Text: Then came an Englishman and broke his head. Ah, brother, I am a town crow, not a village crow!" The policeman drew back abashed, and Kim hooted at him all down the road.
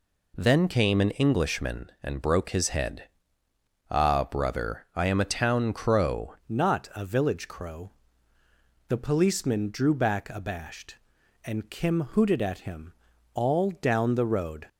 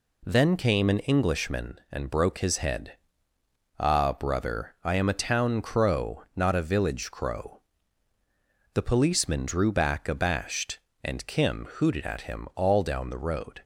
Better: second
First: changes voice at "not"; from 6.4 s on; 8.2 s long // pauses between "him" and "all"; at 12.9 s; 0.42 s long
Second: none

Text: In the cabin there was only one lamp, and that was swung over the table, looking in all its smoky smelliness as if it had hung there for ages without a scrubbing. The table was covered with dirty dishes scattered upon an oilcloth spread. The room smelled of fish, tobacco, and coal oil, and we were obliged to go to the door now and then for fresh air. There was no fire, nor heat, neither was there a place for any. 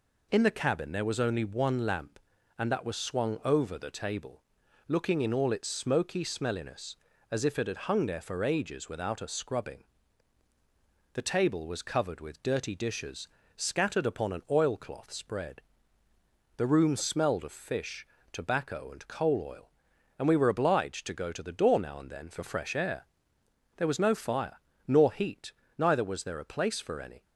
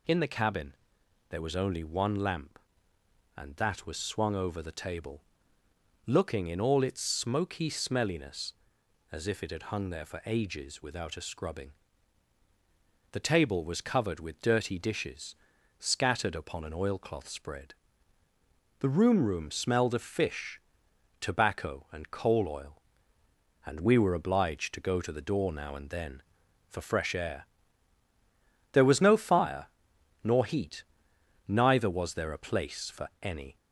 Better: first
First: pauses between "dishes" and "scattered"; slight; at 13.2 s; 0.30 s long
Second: pauses between "cabin" and "there"; noticeable; at 0.7 s; 0.56 s long // pauses between "dishes" and "scattered"; at 15.3 s; 0.42 s long // says "room" twice; at 19.2 s

